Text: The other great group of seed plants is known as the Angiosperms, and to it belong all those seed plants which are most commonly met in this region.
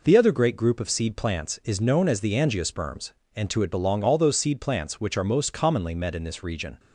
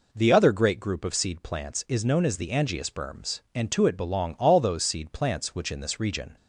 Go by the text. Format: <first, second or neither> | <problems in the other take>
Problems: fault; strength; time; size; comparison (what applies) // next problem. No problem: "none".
first | skips "are most commonly met"; at 5.7 s